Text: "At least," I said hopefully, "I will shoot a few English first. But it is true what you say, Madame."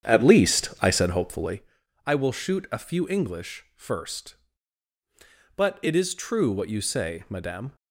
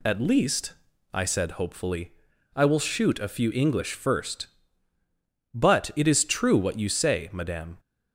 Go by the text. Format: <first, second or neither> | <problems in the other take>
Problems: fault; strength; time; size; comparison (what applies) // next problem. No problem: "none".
second | starts louder than the rest; strong; until 1.6 s; 8.5 dB